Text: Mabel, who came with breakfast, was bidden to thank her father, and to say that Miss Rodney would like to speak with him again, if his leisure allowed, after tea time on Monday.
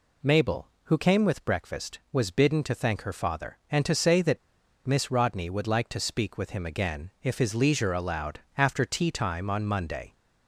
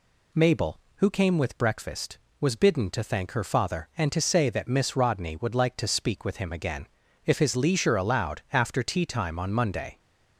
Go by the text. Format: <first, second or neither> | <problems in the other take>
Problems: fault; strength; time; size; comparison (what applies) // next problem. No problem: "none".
second | pauses between "that" and "Miss"; noticeable; at 4.3 s; 0.47 s long